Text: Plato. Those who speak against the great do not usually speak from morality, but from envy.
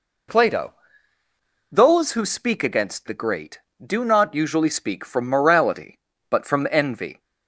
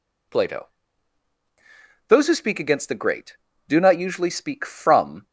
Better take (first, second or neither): first